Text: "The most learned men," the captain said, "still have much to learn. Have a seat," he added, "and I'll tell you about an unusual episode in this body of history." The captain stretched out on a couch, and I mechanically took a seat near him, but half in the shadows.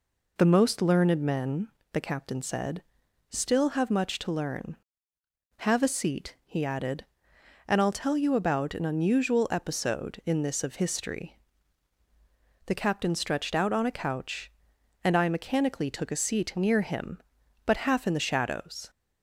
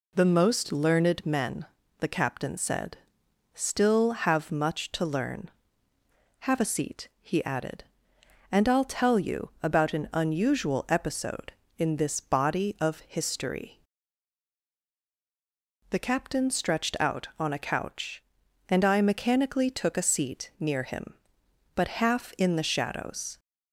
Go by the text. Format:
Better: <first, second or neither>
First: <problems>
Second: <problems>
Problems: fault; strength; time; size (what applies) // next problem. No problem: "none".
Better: second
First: skips "body"; at 10.6 s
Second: none